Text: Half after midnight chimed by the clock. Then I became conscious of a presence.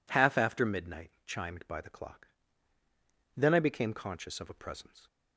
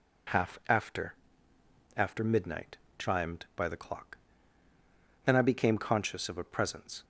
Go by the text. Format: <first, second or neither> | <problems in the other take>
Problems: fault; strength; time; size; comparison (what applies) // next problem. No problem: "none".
first | says "after" twice; at 1.9 s // pauses between "midnight" and "chimed"; slight; at 2.7 s; 0.22 s long; slight in the first